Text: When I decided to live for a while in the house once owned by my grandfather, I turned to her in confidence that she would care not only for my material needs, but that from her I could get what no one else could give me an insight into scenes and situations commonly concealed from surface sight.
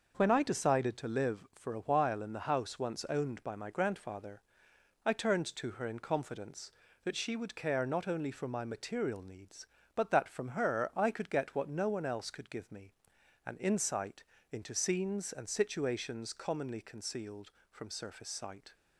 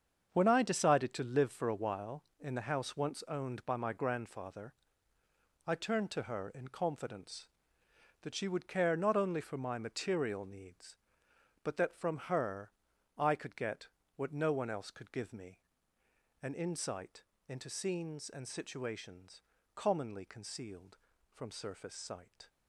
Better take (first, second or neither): first